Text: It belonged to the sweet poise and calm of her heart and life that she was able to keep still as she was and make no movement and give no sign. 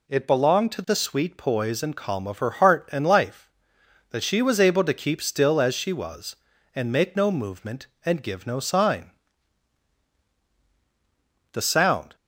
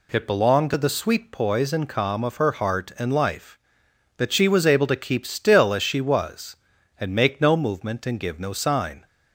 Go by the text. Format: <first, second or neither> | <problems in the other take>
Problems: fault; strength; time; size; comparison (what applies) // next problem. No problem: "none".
second | goes on to say "The sound"; noticeable; from 11.5 s on; 0.62 s long